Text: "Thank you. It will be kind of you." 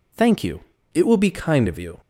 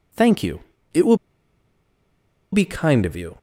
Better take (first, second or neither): first